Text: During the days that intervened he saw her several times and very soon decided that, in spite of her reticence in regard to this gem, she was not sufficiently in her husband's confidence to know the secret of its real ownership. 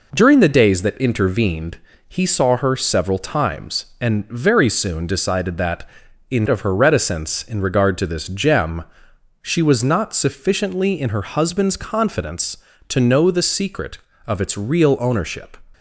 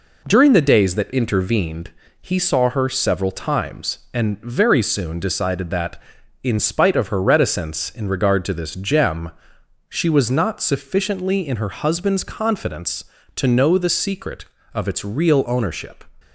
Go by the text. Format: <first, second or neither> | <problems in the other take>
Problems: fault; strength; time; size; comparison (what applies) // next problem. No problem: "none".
second | pauses between "intervened" and "he"; slight; at 1.7 s; 0.30 s long; slight in the second // skips "spite"; at 6.4 s